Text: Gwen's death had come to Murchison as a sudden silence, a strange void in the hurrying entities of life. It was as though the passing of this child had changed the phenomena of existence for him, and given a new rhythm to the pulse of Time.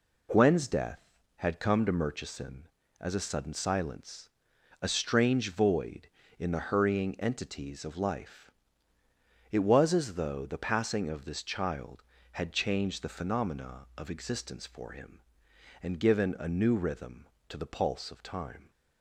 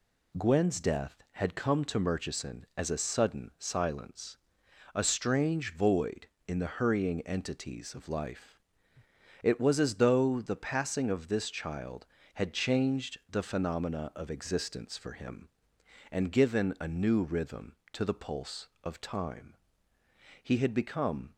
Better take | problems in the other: first | goes on to say "He had become"; noticeable; from 20.4 s on; 0.94 s long

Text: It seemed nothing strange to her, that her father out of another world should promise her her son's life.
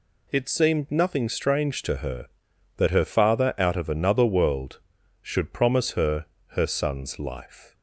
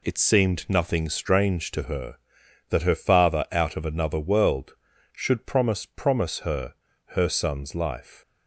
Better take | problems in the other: first | says "promise" twice; at 5.8 s // pauses between "her" and "her"; slight; at 6.7 s; 0.34 s long; slight in the first

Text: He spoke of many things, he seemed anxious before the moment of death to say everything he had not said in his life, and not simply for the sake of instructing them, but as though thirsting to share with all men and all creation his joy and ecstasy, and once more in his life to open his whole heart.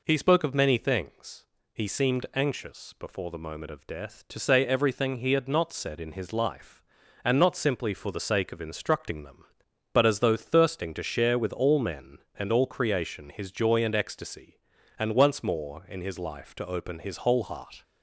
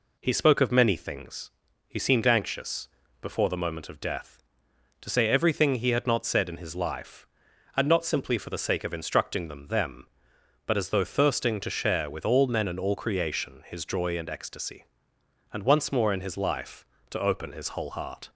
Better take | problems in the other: first | pauses between "anxious" and "before"; slight; at 2.8 s; 0.34 s long // says "them" twice; at 9.6 s

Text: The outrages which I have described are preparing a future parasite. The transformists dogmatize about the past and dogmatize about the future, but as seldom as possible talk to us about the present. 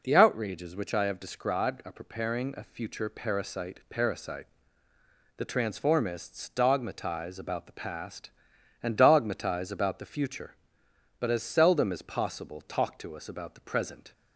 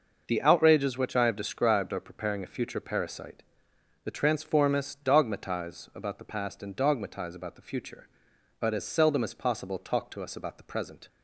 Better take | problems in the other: second | says "parasite" twice; at 3.8 s

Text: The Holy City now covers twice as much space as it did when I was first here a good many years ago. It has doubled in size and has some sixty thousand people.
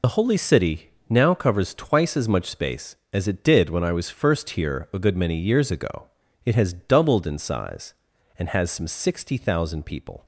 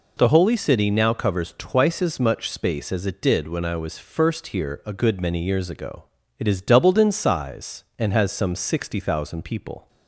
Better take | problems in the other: second | loses the start of "The"; at 0.0 s; 55 ms // pauses between "City" and "now"; slight; at 0.9 s; 0.18 s long

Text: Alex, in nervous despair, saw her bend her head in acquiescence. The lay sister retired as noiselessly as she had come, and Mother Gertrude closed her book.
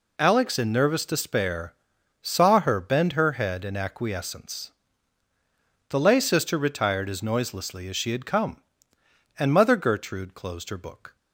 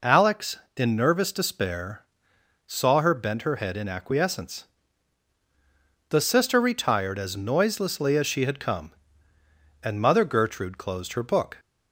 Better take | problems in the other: first | skips "lay"; at 6.2 s

